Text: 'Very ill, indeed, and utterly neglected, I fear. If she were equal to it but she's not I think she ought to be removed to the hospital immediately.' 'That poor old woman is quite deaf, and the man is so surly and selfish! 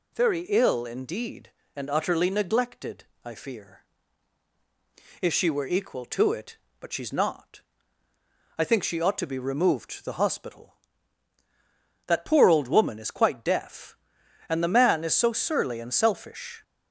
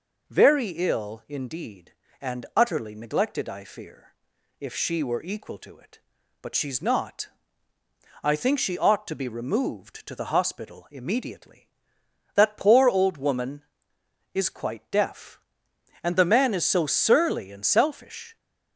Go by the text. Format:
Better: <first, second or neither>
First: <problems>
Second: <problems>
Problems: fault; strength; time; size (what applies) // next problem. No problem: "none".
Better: second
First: pauses between "not" and "I"; noticeable; at 7.6 s; 0.98 s long // skips "immediately"; at 11.4 s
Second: pauses between "not" and "I"; noticeable; at 7.2 s; 0.96 s long